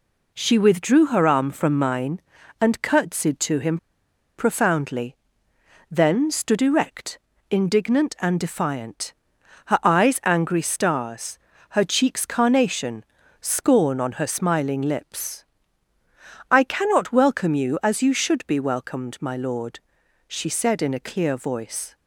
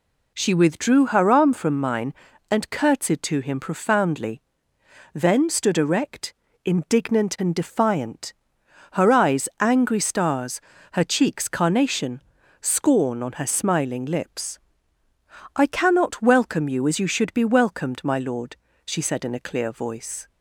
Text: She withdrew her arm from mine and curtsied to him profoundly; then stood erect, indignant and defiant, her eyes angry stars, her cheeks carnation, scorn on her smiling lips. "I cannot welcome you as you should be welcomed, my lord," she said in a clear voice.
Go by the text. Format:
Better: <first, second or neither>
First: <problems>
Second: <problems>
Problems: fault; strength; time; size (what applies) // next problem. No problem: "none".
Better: second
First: pauses between "him" and "profoundly"; noticeable; at 3.7 s; 0.61 s long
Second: none